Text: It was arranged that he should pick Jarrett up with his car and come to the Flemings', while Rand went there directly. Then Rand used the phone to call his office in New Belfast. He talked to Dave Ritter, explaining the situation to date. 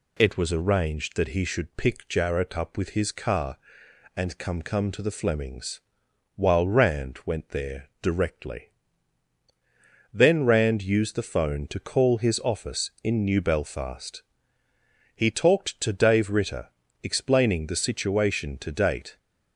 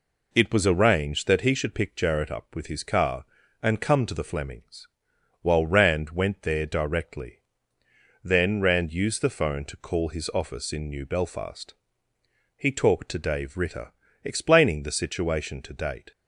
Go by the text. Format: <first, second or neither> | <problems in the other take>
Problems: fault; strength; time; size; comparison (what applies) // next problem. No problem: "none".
second | says "come" twice; at 4.6 s